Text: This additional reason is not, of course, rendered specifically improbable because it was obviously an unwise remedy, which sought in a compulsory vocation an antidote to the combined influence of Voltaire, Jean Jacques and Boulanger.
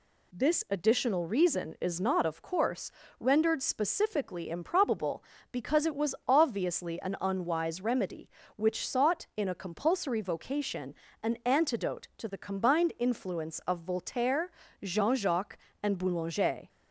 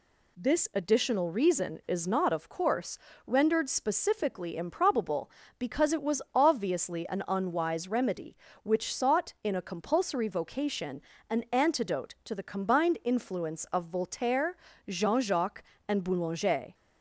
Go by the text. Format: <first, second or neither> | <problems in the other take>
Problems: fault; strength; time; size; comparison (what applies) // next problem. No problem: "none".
neither | pauses between "vocation" and "an"; slight; the same in both